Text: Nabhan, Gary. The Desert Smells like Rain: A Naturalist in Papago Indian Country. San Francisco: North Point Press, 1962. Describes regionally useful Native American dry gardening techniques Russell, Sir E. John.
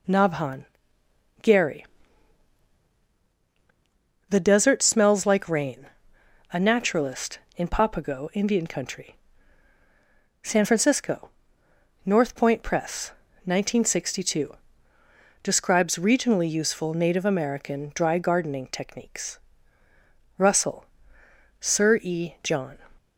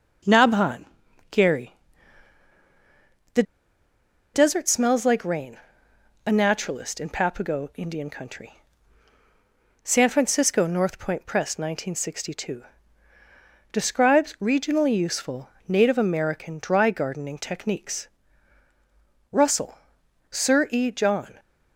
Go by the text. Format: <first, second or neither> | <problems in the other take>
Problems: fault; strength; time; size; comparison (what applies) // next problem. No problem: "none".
first | pauses between "The" and "Desert"; noticeable; at 3.4 s; 0.91 s long // pauses between "useful" and "Native"; slight; at 15.4 s; 0.18 s long // pauses between "techniques" and "Russell"; strong; at 18.0 s; 1.2 s long; also in the first